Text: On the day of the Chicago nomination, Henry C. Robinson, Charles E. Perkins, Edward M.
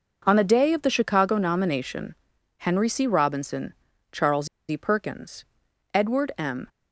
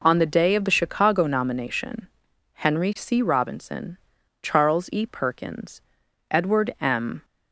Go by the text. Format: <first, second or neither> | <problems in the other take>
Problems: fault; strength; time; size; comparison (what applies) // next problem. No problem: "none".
second | pauses between "Charles" and "E"; slight; at 4.4 s; 0.22 s long